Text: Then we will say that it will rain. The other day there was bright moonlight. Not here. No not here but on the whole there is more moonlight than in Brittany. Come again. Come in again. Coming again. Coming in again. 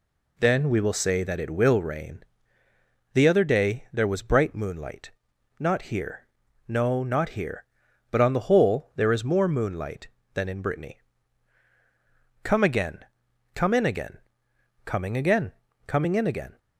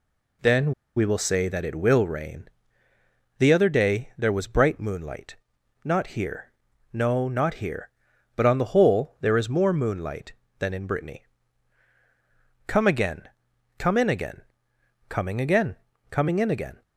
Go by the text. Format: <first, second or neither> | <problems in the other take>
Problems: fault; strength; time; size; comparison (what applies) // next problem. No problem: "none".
first | pauses between "Then" and "we"; slight; at 0.7 s; 0.25 s long